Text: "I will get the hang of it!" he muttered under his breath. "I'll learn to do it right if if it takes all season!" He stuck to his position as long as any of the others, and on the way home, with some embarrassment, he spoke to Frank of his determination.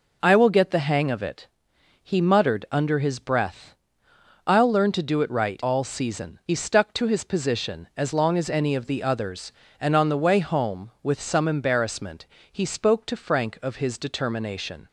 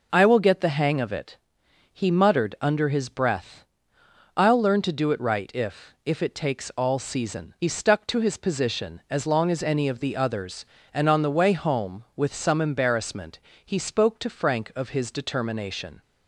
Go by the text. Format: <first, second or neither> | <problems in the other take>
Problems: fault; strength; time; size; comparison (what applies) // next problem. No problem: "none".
second | skips "if if it takes"; at 5.6 s